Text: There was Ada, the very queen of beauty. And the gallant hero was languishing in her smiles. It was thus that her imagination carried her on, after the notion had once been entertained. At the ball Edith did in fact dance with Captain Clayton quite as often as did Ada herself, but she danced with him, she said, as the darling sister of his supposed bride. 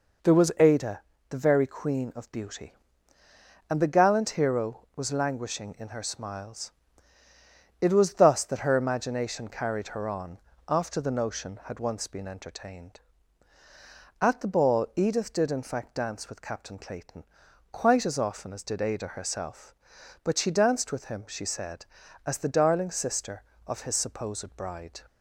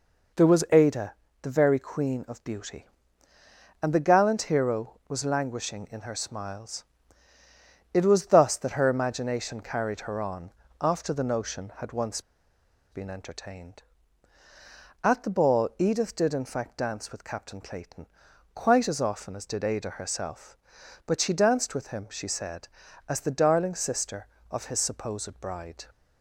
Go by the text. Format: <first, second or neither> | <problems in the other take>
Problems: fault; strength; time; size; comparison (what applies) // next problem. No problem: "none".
first | pauses between "once" and "been"; noticeable; at 12.2 s; 0.68 s long // pauses between "Clayton" and "quite"; noticeable; at 18.0 s; 0.48 s long; noticeable in the first